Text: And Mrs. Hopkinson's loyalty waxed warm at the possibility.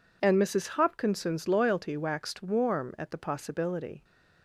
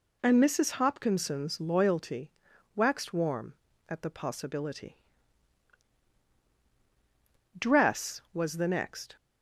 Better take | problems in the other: first | pauses between "loyalty" and "waxed"; at 2.3 s; 0.42 s long // goes on to say "Dress was the next"; from 7.5 s on; 1.5 s long

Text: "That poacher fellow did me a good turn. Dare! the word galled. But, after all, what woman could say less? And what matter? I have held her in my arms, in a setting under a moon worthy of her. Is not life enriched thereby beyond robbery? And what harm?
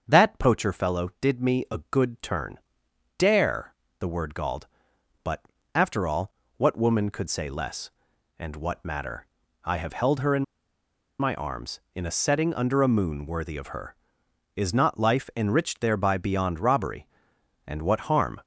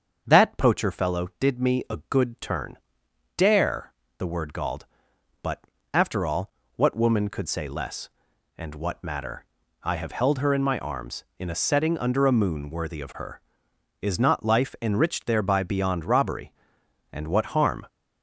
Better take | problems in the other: second | starts louder than the rest; until 1.0 s; 7 dB; also in the second // pauses between "in" and "my"; noticeable; at 10.4 s; 0.76 s long

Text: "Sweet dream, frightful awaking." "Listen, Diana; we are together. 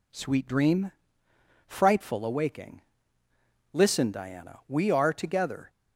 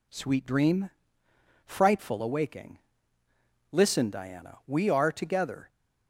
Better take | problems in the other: neither | none

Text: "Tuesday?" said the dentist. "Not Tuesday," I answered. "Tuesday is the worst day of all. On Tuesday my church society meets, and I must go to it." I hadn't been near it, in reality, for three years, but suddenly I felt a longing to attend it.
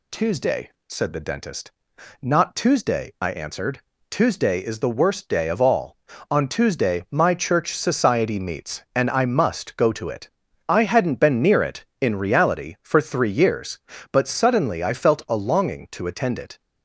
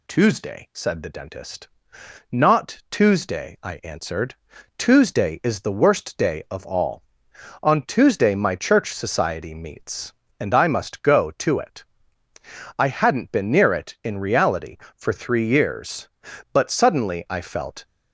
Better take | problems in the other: first | stops before "a longing to attend it"; at 17.8 s

